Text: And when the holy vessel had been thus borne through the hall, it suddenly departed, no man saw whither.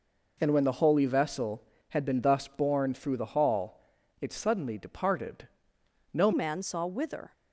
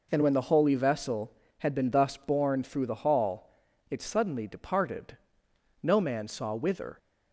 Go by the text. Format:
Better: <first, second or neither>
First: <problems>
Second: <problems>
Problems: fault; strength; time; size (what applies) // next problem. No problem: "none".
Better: second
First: changes voice at "man"; from 6.3 s on; 1.0 s long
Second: none